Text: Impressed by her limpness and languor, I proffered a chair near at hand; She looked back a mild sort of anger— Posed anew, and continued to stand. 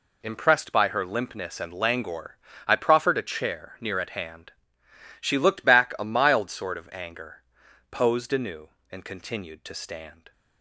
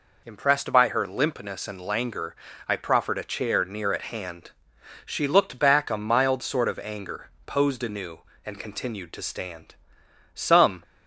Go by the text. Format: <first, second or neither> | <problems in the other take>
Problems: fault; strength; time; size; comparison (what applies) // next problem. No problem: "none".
first | goes on to say "Some"; slight; from 10.3 s on; 0.48 s long